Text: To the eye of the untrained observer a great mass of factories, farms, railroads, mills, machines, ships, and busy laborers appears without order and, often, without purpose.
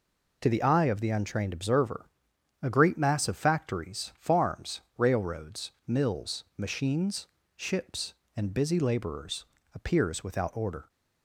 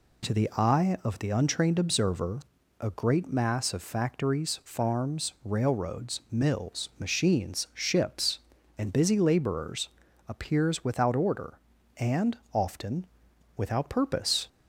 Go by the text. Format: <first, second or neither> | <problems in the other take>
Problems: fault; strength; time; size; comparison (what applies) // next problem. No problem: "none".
second | pauses between "observer" and "a"; noticeable; at 2.0 s; 0.56 s long; also in the second // pauses between "laborers" and "appears"; slight; at 9.4 s; 0.28 s long; slight in the second // stops before "and often without purpose"; at 10.8 s